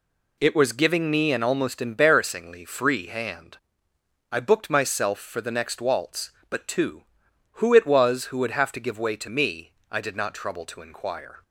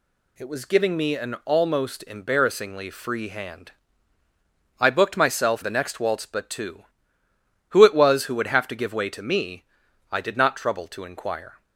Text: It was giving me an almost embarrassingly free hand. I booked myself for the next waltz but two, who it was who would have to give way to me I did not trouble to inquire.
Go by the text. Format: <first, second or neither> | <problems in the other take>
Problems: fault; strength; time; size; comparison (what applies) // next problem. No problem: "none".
first | skips "for"; at 5.6 s // pauses between "me" and "I"; noticeable; at 9.6 s; 0.50 s long; slight in the first